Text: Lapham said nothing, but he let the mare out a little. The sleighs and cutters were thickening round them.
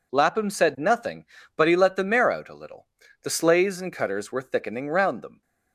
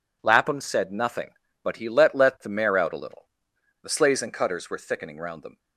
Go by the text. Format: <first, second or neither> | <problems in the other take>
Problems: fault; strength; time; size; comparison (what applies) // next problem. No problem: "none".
first | says "let" twice; at 2.1 s